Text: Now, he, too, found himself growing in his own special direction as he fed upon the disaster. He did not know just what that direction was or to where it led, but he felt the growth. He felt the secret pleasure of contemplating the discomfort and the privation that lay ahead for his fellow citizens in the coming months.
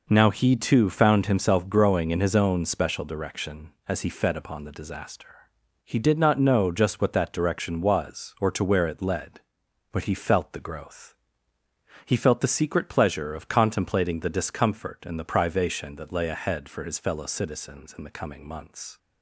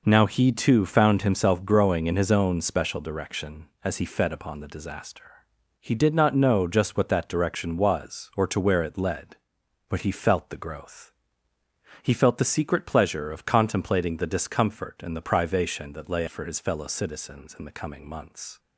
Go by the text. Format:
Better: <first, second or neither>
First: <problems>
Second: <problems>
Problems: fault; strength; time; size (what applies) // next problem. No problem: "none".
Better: first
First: none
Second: skips "ahead"; at 16.2 s